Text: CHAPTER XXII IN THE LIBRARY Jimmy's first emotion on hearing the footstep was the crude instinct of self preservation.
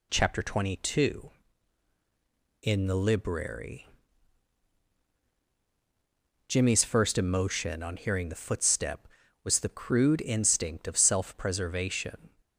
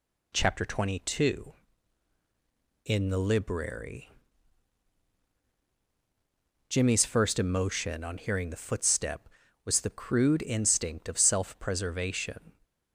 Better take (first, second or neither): neither